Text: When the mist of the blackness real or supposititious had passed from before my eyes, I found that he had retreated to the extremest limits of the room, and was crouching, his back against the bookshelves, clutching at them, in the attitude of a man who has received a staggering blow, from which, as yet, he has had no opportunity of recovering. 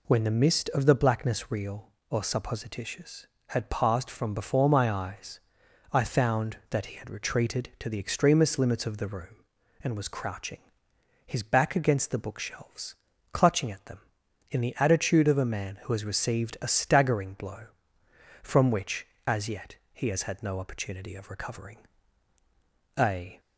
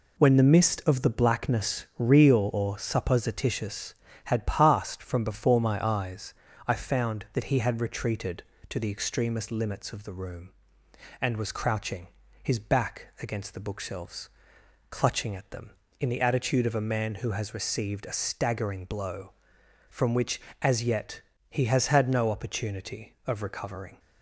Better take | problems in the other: second | goes on to say "A"; slight; from 22.9 s on; 0.42 s long

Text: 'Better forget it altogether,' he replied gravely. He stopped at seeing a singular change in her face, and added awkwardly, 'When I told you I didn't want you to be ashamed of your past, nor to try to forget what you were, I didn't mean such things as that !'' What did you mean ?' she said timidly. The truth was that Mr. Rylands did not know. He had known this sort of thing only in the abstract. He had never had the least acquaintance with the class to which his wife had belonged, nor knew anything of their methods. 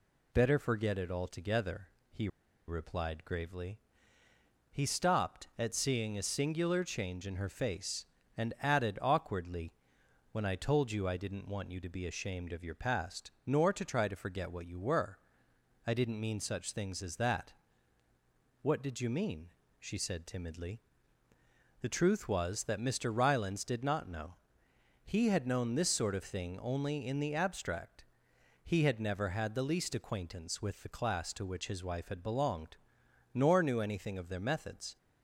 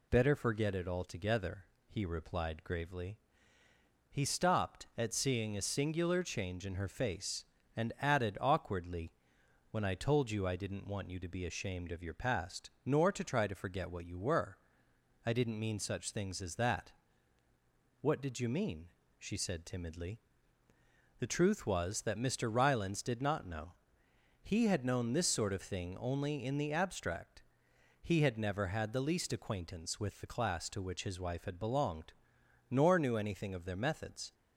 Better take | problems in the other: second | pauses between "he" and "replied"; at 2.2 s; 0.40 s long

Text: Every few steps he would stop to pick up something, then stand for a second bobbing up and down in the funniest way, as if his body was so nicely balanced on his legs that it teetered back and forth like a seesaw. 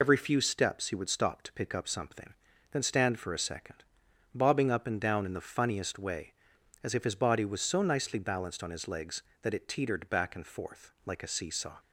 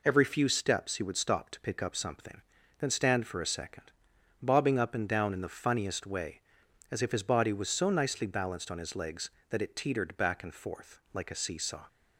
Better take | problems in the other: second | loses the start of "Every"; at 0.0 s; 40 ms // pauses between "second" and "bobbing"; noticeable; at 3.8 s; 0.50 s long; noticeable in the second

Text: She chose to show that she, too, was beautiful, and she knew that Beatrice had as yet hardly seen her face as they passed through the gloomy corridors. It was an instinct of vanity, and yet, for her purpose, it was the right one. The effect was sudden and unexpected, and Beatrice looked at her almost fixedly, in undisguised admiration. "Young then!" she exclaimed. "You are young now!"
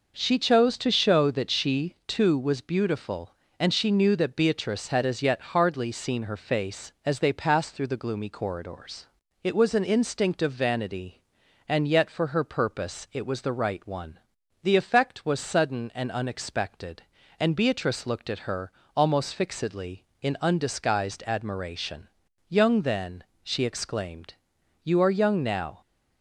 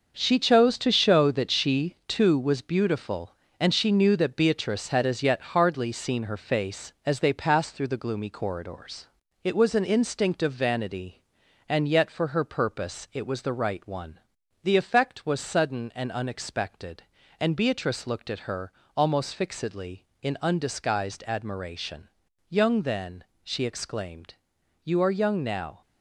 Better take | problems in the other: first | gets quieter; strong; throughout; 8 dB // pauses between "her" and "almost"; slight; at 18.7 s; 0.24 s long; slight in the first

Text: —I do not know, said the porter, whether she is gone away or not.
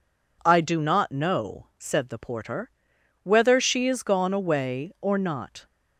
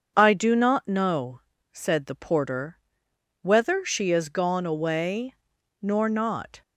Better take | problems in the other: first | starts louder than the rest; until 1.1 s; 7 dB // says "nor" for "or"; at 5.8 s

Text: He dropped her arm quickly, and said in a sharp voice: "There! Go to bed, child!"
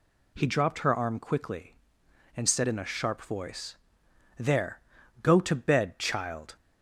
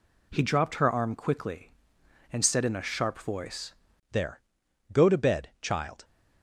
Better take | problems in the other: first | changes voice at "There"; from 4.1 s on; 1.9 s long

